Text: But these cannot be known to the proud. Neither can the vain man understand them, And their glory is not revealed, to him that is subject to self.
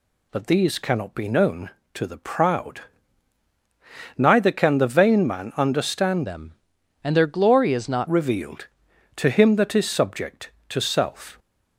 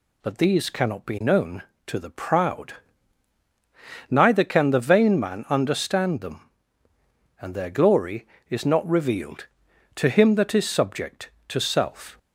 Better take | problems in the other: second | changes voice from "them" to "not"; from 6.2 to 8.0 s; 1.8 s long

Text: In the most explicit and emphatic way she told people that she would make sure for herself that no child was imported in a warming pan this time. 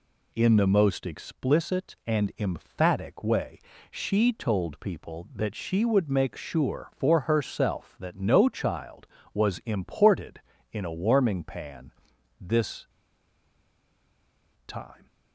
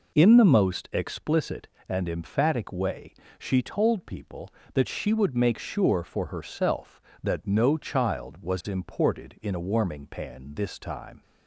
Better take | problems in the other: second | pauses between "way" and "she"; slight; at 3.5 s; 0.32 s long; slight in the second // pauses between "pan" and "this"; noticeable; at 11.9 s; 0.48 s long // pauses between "this" and "time"; strong; at 12.8 s; 1.7 s long

